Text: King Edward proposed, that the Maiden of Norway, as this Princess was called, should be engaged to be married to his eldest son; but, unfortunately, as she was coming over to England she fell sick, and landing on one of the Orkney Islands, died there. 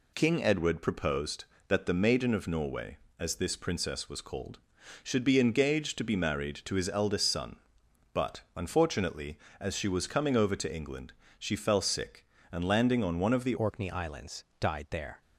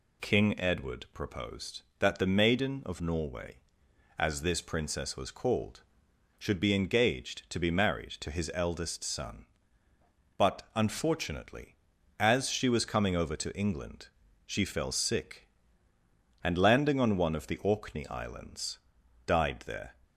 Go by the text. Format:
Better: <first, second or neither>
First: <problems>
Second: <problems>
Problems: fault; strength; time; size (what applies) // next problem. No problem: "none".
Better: second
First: pauses between "England" and "she"; slight; at 11.1 s; 0.28 s long // changes voice at "Orkney"; from 13.5 s on; 1.7 s long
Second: pauses between "England" and "she"; slight; at 14.0 s; 0.36 s long